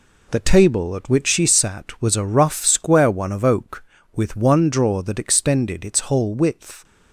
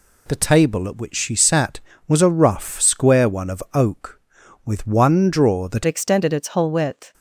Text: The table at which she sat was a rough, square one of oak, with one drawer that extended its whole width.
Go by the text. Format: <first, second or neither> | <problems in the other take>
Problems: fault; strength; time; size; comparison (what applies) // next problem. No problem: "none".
first | changes voice at "extended"; from 5.8 s on; 1.3 s long